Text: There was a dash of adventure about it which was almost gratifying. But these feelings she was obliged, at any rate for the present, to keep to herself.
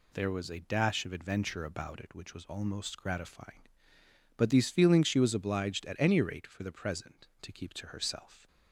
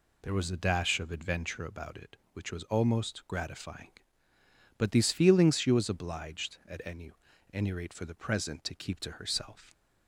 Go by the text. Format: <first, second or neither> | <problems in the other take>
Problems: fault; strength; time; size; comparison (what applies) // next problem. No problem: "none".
first | says "any" twice; at 7.5 s